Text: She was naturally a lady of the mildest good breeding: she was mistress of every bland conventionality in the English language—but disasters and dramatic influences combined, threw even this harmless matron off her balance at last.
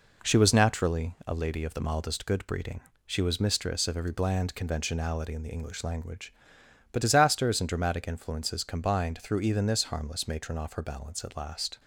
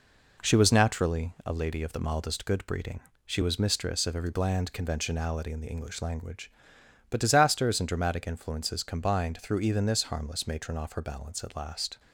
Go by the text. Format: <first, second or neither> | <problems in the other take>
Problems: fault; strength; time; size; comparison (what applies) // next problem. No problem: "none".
neither | none